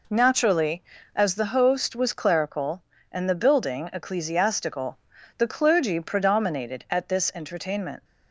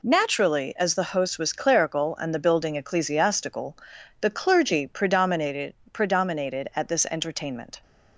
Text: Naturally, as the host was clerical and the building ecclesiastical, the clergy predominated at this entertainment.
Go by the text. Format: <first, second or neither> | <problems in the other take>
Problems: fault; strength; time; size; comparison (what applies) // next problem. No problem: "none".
first | says "predominated" twice; at 5.9 s